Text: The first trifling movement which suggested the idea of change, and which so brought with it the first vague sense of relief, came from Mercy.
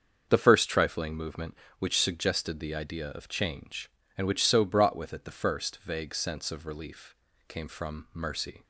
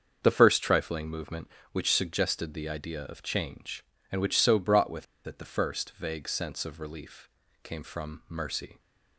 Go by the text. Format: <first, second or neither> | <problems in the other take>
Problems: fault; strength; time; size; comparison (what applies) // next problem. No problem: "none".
first | starts louder than the rest; until 1.2 s; 7 dB; also in the first // pauses between "with" and "it"; slight; at 5.0 s; 0.21 s long